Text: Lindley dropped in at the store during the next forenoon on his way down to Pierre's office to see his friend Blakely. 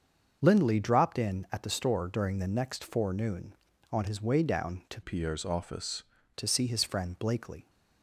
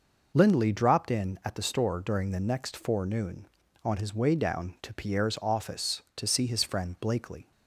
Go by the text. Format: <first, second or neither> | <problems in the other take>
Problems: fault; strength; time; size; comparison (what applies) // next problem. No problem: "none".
second | starts louder than the rest; until 1.4 s; 6.5 dB // changes voice from "Pierre's" to "office"; from 5.0 to 6.0 s; 1.0 s long